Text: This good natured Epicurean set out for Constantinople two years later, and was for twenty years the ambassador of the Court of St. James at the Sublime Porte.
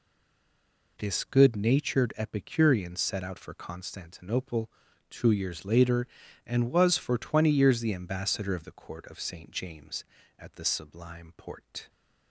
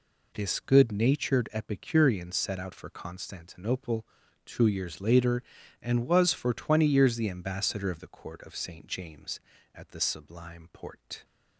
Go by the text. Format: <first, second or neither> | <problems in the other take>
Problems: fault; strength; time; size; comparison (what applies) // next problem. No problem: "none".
second | stays silent before the first word; until 0.9 s; 0.9 s long // pauses between "Constantinople" and "two"; at 4.7 s; 0.40 s long; also in the second